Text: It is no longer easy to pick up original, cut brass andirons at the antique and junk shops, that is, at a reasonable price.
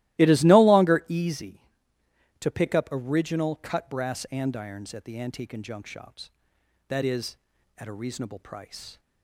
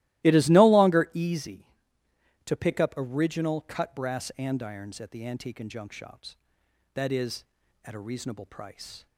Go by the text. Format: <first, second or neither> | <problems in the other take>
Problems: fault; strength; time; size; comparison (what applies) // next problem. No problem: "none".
neither | starts louder than the rest; strong; the same in both